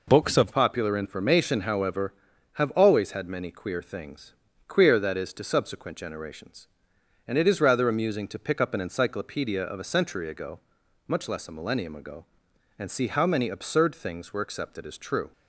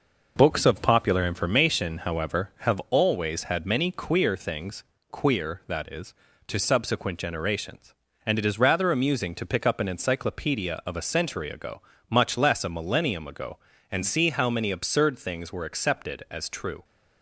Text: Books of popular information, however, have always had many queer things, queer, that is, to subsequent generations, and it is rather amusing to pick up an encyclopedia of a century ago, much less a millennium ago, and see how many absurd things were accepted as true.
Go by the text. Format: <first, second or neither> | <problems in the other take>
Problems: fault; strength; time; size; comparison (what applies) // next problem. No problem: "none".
second | changes voice at "popular"; from 0.5 s on; 14.8 s long